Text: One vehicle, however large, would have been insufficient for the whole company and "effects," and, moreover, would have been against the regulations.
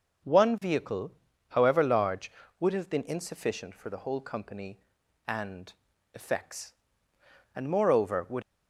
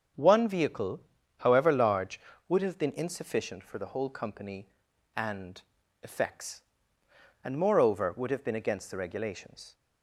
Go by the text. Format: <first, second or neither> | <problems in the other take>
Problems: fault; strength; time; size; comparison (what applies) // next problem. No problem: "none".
second | starts louder than the rest; until 1.6 s; 6.5 dB; strong in the second // pauses between "and" and "effects"; at 5.7 s; 0.42 s long; also in the second // stops before "have been against the regulations"; at 8.4 s